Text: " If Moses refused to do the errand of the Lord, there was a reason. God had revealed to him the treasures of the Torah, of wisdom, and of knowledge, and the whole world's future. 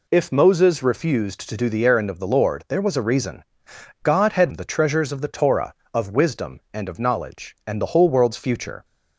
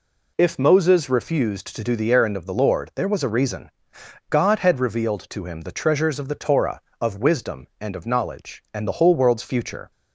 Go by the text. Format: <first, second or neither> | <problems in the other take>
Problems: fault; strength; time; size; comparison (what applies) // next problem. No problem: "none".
second | skips "revealed to him"; at 4.5 s